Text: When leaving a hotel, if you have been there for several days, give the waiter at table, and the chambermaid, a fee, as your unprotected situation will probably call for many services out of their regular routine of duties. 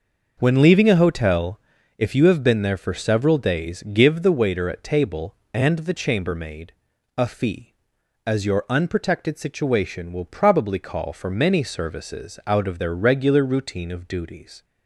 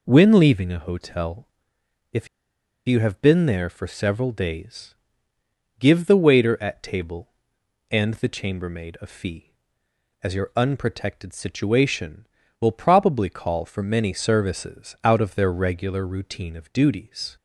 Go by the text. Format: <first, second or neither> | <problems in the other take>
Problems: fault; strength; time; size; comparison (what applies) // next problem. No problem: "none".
first | pauses between "if" and "you"; noticeable; at 2.2 s; 0.60 s long